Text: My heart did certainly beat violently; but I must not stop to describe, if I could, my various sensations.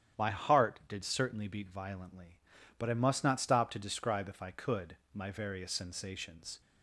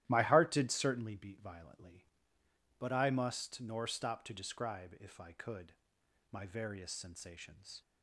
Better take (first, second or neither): first